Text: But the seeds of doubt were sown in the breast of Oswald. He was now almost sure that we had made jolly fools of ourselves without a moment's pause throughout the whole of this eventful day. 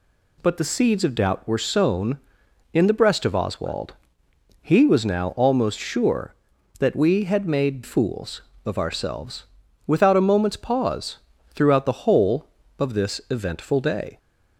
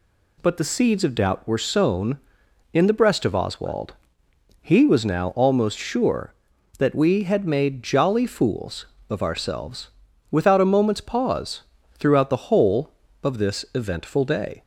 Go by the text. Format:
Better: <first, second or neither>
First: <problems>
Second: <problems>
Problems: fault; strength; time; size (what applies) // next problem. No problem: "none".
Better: second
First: skips "jolly"; at 7.8 s // pauses between "ourselves" and "without"; at 9.4 s; 0.42 s long // pauses between "pause" and "throughout"; slight; at 11.1 s; 0.32 s long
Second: pauses between "ourselves" and "without"; at 9.8 s; 0.42 s long // pauses between "pause" and "throughout"; slight; at 11.6 s; 0.32 s long